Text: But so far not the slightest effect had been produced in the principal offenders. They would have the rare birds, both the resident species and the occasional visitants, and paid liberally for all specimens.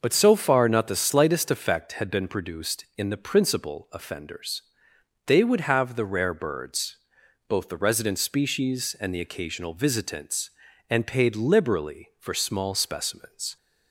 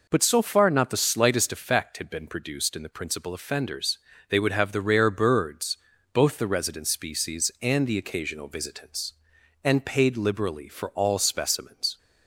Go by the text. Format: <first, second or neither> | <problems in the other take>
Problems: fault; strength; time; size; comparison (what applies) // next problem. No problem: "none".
second | starts louder than the rest; noticeable; until 1.0 s; 6 dB // says "small" for "all"; at 12.3 s